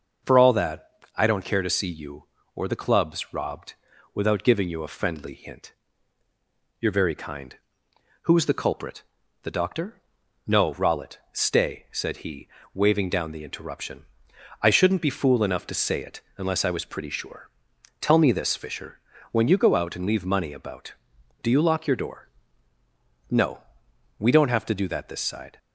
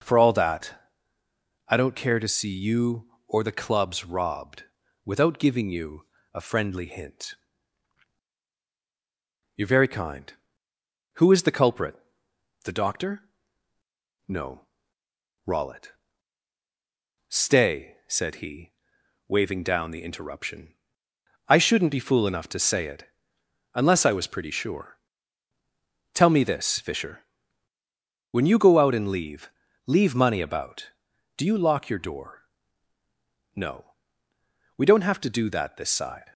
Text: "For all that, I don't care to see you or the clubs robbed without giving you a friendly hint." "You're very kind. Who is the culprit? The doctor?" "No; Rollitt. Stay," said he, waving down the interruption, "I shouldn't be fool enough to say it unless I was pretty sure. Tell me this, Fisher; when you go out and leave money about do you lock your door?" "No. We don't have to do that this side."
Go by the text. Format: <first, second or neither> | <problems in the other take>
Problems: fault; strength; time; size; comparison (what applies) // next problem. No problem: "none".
first | pauses between "robbed" and "without"; at 4.6 s; 0.40 s long; also in the first // pauses between "you" and "a"; slight; at 6.0 s; 0.28 s long // pauses between "it" and "unless"; noticeable; at 23.0 s; 0.64 s long; slight in the first // says "leave" twice; at 29.8 s